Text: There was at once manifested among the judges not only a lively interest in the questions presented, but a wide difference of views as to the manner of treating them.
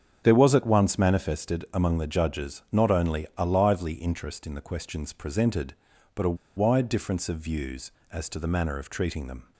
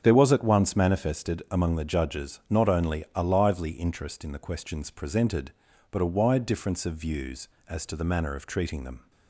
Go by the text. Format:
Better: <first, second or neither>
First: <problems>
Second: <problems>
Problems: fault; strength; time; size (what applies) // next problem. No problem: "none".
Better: second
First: starts louder than the rest; strong; until 1.2 s; 7.5 dB // pauses between "a" and "wide"; slight; at 6.3 s; 0.20 s long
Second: starts louder than the rest; strong; until 1.0 s; 8 dB